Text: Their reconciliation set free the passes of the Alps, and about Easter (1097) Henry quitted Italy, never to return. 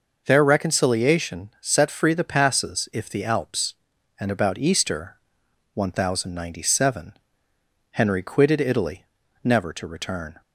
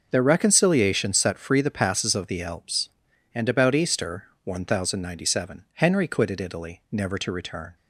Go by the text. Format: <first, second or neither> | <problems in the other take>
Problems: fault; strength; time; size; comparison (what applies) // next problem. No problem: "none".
second | says "if" for "of"; at 2.9 s